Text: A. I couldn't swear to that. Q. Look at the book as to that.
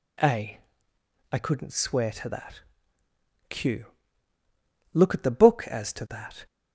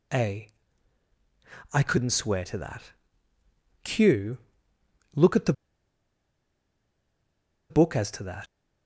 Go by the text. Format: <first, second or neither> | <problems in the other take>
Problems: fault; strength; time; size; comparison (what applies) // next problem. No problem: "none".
first | pauses between "the" and "book"; strong; at 5.5 s; 2.1 s long